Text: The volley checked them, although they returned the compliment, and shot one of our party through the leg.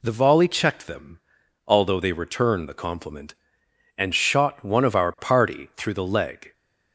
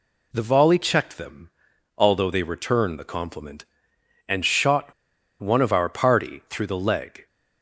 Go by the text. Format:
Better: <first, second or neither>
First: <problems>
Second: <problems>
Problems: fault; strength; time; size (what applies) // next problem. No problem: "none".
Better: first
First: none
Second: pauses between "shot" and "one"; noticeable; at 4.9 s; 0.48 s long